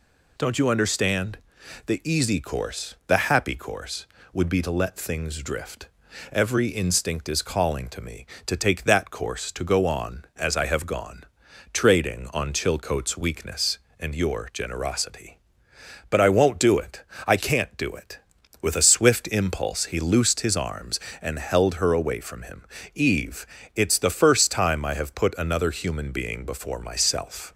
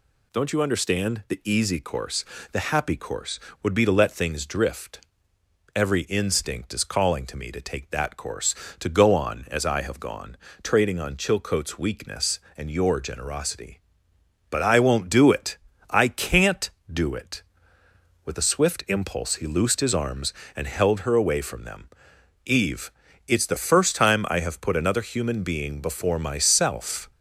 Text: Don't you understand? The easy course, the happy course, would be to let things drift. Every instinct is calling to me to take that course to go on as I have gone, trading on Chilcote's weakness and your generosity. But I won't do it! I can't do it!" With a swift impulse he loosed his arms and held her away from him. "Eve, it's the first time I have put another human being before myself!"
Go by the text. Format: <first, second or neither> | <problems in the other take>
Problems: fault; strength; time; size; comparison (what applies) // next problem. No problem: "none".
first | says "them" for "him"; at 21.6 s